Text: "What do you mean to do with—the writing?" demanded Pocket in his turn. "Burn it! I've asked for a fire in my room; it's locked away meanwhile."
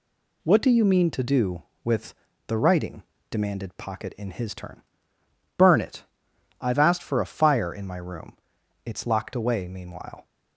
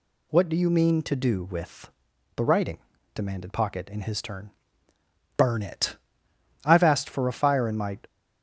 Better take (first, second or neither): first